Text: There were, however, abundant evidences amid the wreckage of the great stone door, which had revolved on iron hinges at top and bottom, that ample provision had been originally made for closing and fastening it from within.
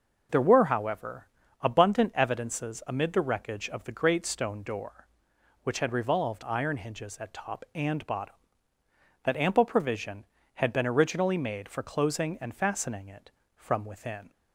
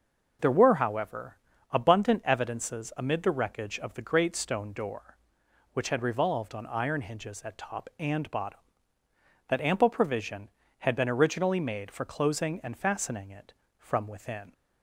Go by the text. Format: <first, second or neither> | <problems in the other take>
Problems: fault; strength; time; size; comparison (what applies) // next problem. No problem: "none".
second | skips "on"; at 6.4 s